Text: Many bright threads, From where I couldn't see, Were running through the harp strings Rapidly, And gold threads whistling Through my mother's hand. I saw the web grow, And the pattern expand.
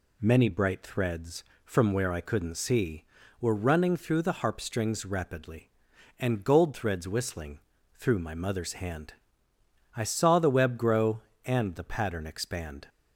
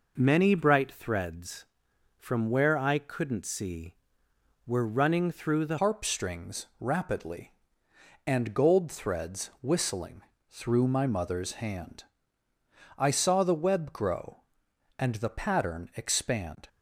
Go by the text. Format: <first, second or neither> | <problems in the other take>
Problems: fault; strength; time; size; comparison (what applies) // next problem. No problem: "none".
first | changes voice at "harp"; from 5.7 s on; 10.9 s long // pauses between "whistling" and "Through"; slight; at 10.2 s; 0.28 s long; slight in the first